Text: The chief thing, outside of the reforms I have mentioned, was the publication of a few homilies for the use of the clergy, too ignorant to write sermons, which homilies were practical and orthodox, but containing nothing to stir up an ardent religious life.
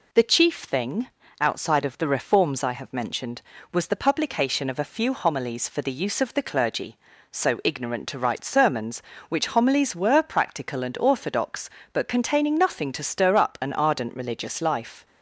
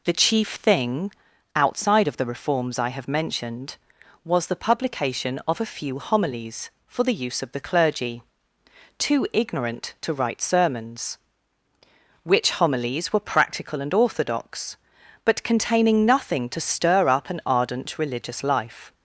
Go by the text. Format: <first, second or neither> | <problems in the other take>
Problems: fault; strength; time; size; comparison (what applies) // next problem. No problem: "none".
second | says "so" for "too"; at 7.3 s